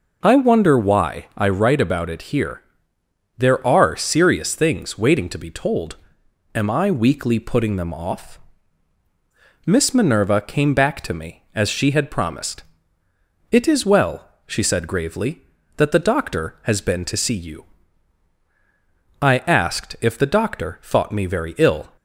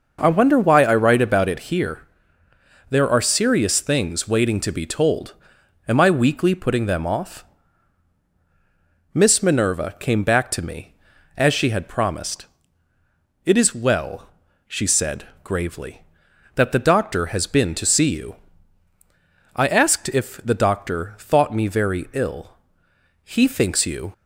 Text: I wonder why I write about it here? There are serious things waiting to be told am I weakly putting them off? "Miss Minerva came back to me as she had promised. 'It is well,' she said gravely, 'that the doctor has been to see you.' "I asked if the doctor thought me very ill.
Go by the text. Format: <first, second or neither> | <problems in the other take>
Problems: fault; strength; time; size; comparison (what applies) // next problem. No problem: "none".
first | pauses between "told" and "am"; noticeable; at 5.3 s; 0.54 s long; noticeable in the first // pauses between "said" and "gravely"; slight; at 15.2 s; 0.16 s long // goes on to say "He thinks you"; noticeable; from 23.2 s on; 0.88 s long